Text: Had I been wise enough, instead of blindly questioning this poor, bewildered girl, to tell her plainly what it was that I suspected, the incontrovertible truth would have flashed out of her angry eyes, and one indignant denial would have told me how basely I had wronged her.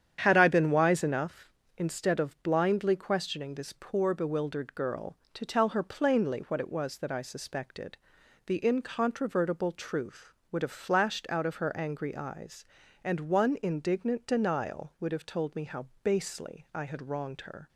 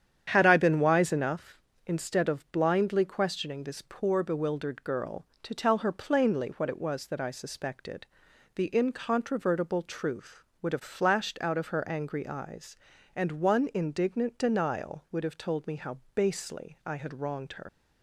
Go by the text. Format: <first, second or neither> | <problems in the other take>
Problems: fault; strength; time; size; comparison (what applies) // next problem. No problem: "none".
first | starts louder than the rest; strong; until 1.3 s; 9 dB; strong in the first // pauses between "how" and "basely"; slight; at 15.9 s; 0.16 s long; slight in the first // leaves "her" unfinished; at 17.6 s; 105 ms